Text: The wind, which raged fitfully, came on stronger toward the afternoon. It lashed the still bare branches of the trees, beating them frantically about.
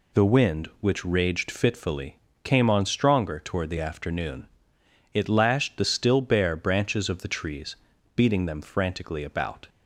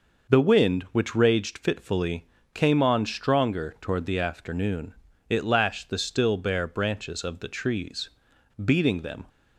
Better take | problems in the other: first | stops before "frantically about"; at 9.2 s

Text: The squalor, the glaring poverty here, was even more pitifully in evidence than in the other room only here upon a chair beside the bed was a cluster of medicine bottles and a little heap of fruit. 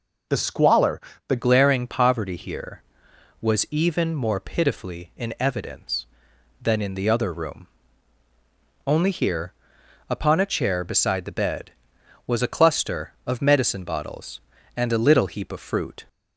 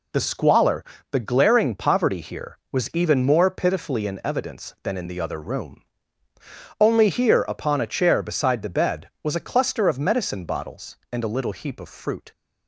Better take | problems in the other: second | changes voice at "glaring"; from 1.3 s on; 14.7 s long // pauses between "room" and "only"; at 7.6 s; 1.1 s long; noticeable in the second // pauses between "here" and "upon"; noticeable; at 9.5 s; 0.56 s long

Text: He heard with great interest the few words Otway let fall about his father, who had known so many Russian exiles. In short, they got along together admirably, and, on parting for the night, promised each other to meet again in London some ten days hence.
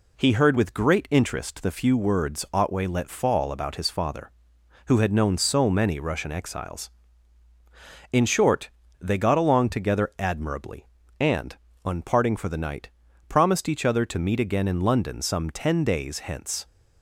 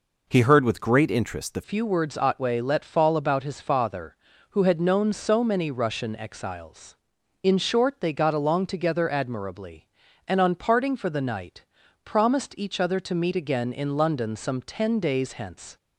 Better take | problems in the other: first | changes voice at "few"; from 1.6 s on; 14.1 s long

